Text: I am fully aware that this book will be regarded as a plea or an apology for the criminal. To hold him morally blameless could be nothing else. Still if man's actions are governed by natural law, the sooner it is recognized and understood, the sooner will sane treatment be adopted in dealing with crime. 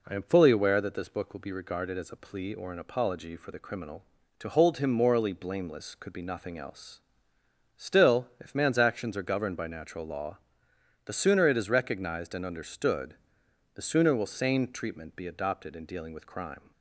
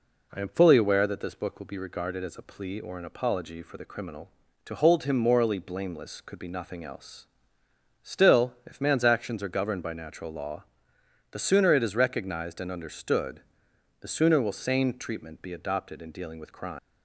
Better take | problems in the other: first | leaves "crime" unfinished; at 16.7 s; 185 ms

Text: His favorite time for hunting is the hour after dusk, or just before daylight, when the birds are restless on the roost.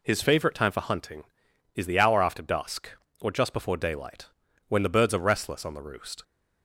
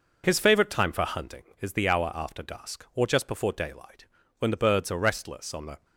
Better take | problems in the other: first | stops before "roost"; at 5.8 s

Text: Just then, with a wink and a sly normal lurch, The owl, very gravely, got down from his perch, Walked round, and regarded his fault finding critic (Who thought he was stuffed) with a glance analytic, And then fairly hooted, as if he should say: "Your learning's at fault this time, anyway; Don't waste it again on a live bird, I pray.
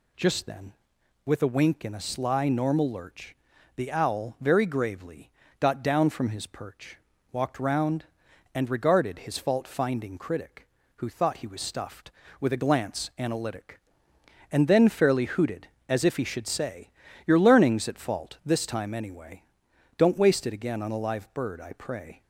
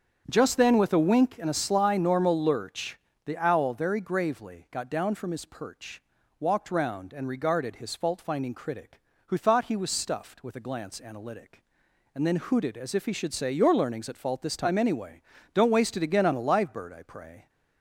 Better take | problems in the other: first | starts louder than the rest; strong; until 1.3 s; 7.5 dB // skips "fairly"; at 12.3 s

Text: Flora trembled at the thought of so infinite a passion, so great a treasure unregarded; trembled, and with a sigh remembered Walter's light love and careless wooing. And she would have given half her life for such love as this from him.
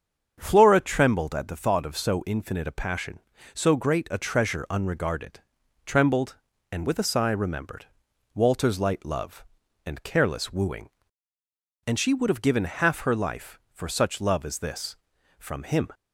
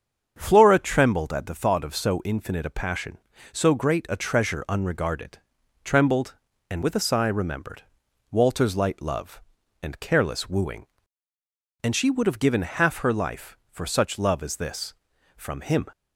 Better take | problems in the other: neither | starts louder than the rest; strong; the same in both // pauses between "remembered" and "Walter's"; noticeable; the same in both

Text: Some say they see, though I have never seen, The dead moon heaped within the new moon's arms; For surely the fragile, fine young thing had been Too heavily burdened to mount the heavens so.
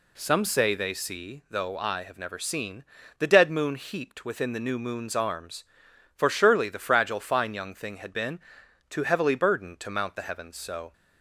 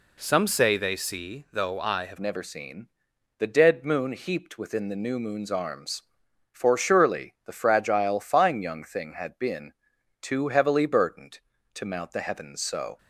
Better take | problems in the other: first | changes voice at "never"; from 2.1 s on; 10.8 s long // pauses between "been" and "Too"; noticeable; at 9.7 s; 0.48 s long; noticeable in the first

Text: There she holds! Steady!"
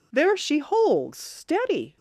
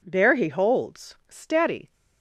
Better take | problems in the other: first | says "he" for "she"; at 0.3 s

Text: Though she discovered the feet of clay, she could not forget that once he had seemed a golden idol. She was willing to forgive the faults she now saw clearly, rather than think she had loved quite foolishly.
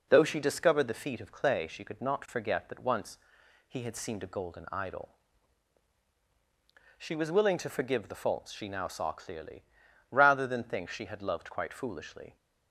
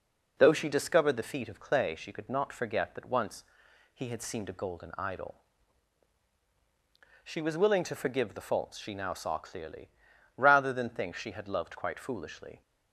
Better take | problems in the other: neither | pauses between "once" and "he"; noticeable; the same in both

